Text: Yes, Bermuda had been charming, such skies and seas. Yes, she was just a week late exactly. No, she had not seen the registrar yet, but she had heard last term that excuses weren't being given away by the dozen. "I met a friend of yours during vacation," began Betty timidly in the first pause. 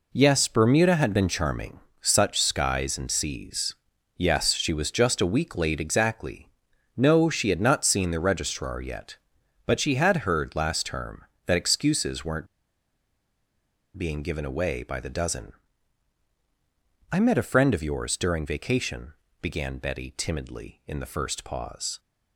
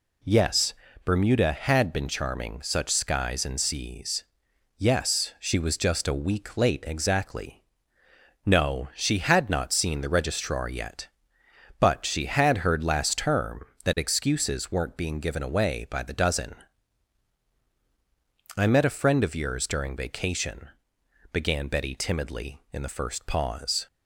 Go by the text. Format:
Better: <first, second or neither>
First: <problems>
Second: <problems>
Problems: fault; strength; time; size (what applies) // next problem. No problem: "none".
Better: second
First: pauses between "weren't" and "being"; strong; at 12.4 s; 1.5 s long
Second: none